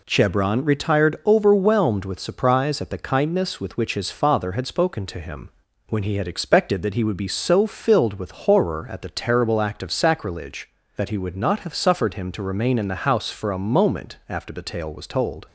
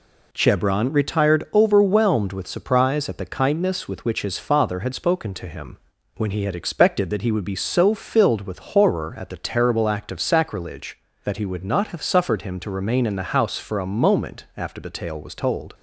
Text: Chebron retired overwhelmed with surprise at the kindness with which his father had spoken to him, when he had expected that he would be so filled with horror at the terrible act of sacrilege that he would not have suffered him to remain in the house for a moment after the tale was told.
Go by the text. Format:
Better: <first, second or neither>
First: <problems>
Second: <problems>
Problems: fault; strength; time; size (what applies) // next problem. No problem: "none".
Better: neither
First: none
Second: none